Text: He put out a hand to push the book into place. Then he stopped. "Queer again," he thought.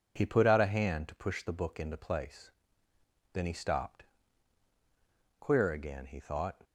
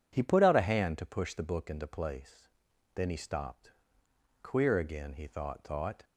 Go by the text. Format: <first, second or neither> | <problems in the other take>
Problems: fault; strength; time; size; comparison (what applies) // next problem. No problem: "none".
first | says "thought" twice; at 5.6 s